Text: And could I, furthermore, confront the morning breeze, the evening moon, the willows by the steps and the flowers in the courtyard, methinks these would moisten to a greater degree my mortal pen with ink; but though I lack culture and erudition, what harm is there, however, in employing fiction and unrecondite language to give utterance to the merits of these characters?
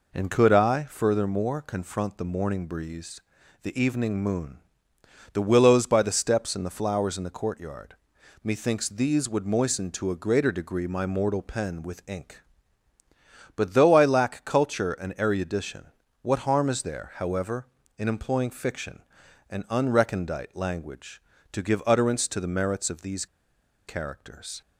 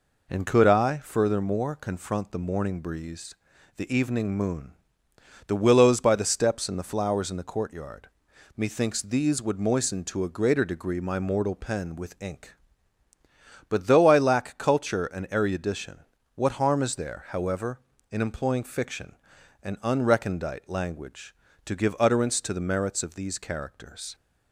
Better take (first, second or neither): second